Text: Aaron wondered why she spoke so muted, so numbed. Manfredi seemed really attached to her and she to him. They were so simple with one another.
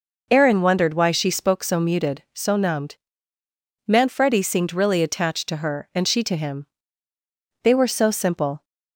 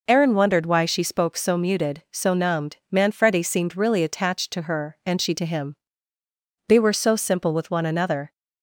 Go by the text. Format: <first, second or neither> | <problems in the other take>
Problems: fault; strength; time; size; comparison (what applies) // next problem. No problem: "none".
second | stops before "with one another"; at 8.6 s